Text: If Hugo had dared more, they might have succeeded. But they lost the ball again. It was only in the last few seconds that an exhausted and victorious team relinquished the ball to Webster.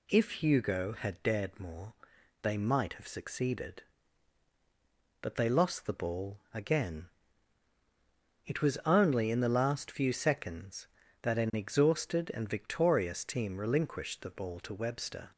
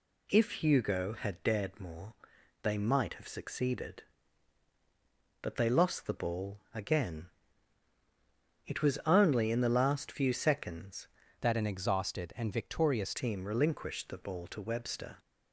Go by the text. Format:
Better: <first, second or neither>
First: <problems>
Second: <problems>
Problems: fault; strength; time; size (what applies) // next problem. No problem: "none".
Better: first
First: none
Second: changes voice from "that" to "victorious"; from 11.3 to 13.1 s; 1.8 s long